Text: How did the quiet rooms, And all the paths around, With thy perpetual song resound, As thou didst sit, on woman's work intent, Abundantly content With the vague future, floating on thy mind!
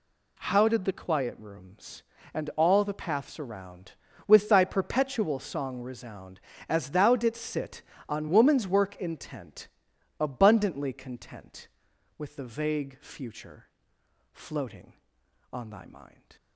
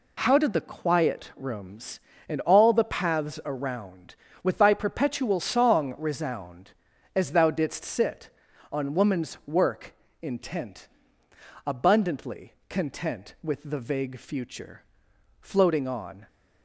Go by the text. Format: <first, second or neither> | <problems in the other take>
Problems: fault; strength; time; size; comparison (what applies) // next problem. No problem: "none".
first | pauses between "work" and "intent"; slight; at 9.9 s; 0.30 s long // pauses between "Abundantly" and "content"; slight; at 12.5 s; 0.16 s long // stops before "thy mind"; at 16.2 s